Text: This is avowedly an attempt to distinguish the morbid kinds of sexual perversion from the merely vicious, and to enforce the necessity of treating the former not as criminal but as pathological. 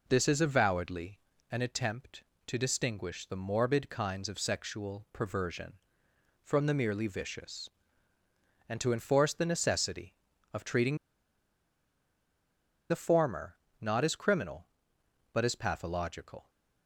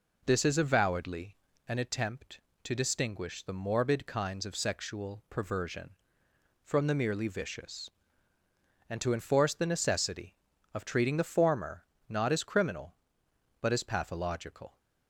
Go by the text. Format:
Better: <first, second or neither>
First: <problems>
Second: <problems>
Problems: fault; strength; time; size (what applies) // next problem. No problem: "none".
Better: second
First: pauses between "avowedly" and "an"; slight; at 1.1 s; 0.32 s long // pauses between "treating" and "the"; strong; at 10.9 s; 1.9 s long // pauses between "former" and "not"; slight; at 13.5 s; 0.26 s long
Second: pauses between "avowedly" and "an"; slight; at 1.3 s; 0.32 s long // pauses between "former" and "not"; slight; at 11.8 s; 0.26 s long